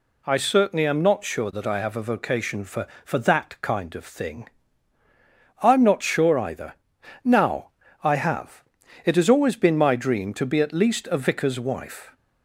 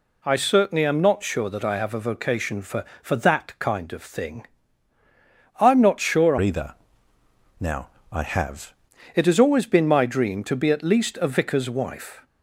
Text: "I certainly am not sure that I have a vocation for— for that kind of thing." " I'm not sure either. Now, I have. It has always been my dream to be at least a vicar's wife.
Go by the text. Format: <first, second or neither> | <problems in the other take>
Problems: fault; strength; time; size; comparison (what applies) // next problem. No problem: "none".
first | changes voice from "either" to "have"; from 6.4 to 8.7 s; 2.3 s long